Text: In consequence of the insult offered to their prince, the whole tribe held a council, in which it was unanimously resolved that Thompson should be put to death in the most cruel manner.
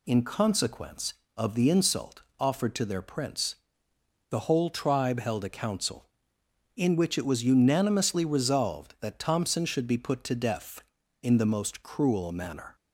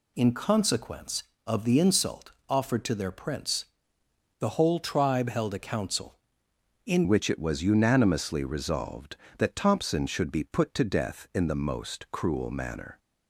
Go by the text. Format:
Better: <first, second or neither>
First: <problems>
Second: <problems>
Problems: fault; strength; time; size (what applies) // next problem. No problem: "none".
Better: first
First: pauses between "insult" and "offered"; slight; at 2.2 s; 0.16 s long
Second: pauses between "insult" and "offered"; slight; at 2.3 s; 0.16 s long // changes voice at "which"; from 7.0 s on; 5.9 s long